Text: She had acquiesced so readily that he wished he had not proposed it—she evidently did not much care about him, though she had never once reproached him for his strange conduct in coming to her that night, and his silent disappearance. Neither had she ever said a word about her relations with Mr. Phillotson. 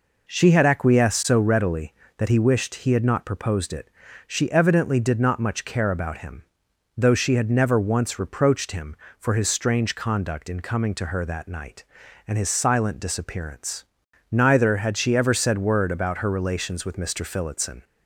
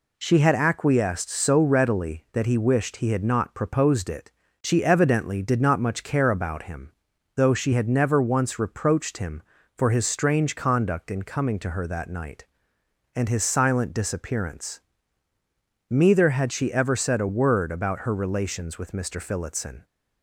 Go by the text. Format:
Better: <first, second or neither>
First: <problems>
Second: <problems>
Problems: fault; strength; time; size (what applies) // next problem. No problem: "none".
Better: second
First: skips "a"; at 15.5 s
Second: none